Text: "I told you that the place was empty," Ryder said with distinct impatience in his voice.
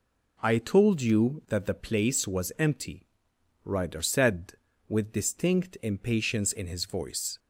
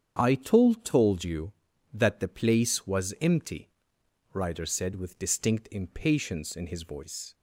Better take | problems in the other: first | starts louder than the rest; strong; until 1.2 s; 8 dB // says "told" twice; at 0.8 s

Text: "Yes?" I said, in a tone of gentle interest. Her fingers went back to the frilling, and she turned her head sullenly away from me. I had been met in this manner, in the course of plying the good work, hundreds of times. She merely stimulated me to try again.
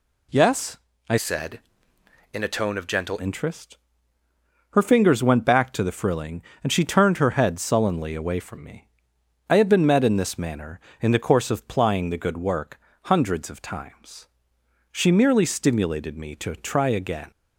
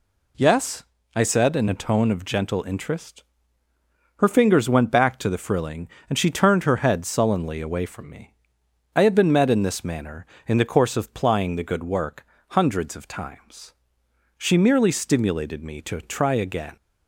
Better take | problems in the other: second | changes voice from "said" to "gentle"; from 1.1 to 3.1 s; 2.0 s long

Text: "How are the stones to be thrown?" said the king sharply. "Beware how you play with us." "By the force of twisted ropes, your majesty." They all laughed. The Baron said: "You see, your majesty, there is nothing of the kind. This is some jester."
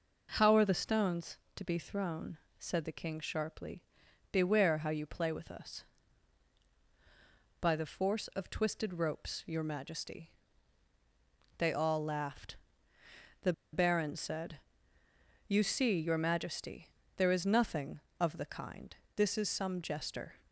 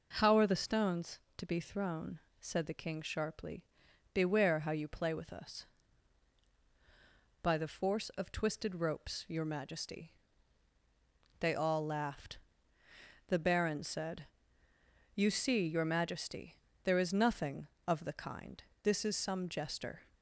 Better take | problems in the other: second | pauses between "The" and "Baron"; slight; at 13.5 s; 0.21 s long

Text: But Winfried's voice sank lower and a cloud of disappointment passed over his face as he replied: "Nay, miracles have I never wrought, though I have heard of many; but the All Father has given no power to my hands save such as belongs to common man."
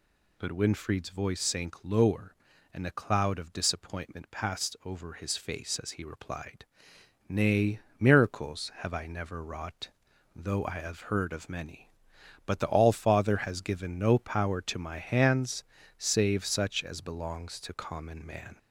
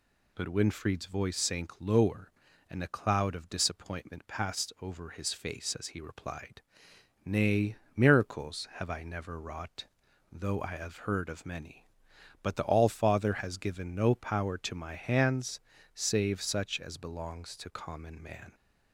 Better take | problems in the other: second | gets louder; slight; throughout; 3 dB // pauses between "hands" and "save"; slight; at 15.6 s; 0.34 s long; slight in the second

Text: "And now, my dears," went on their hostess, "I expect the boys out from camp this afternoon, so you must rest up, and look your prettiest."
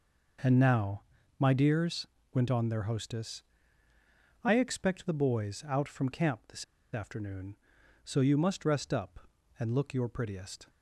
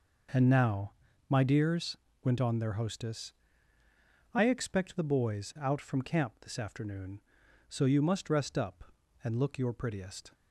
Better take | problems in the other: second | pauses between "this" and "afternoon"; slight; at 6.6 s; 0.29 s long

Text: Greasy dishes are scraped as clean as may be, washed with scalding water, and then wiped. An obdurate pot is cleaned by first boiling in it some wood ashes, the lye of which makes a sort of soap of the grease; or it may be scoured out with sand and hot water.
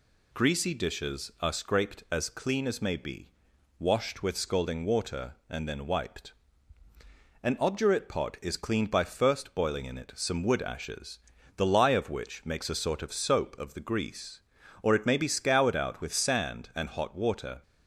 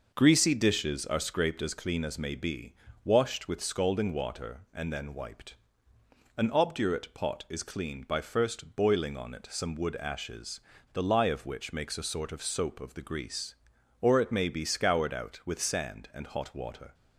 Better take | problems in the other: first | says "on" for "in"; at 9.1 s

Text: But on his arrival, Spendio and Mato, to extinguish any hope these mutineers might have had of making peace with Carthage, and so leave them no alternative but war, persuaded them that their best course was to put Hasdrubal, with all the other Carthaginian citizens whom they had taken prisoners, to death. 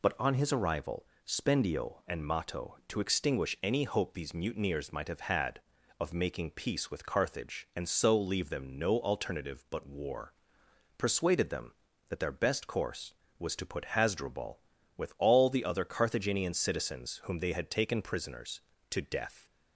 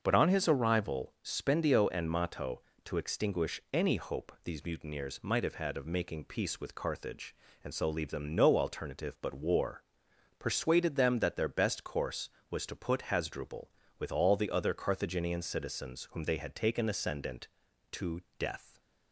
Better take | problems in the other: first | starts louder than the rest; until 1.0 s; 6.5 dB // says "ascendant" for "prisoners"; at 16.8 s // pauses between "to" and "death"; slight; at 18.2 s; 0.18 s long

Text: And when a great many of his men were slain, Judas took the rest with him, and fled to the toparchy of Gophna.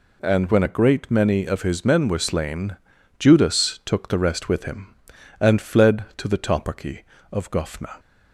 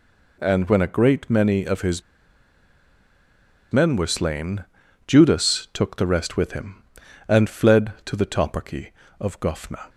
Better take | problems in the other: first | pauses between "his" and "men"; strong; at 2.0 s; 1.7 s long

